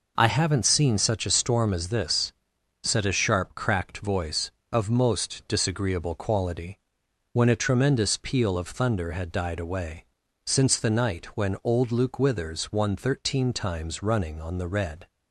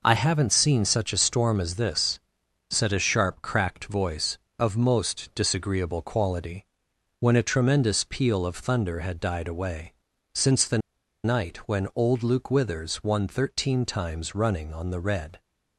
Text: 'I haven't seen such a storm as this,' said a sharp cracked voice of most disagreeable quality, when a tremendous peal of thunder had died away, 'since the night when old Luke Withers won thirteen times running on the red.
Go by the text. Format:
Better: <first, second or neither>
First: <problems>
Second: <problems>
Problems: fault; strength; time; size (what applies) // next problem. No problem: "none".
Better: first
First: none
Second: pauses between "the" and "night"; at 10.7 s; 0.45 s long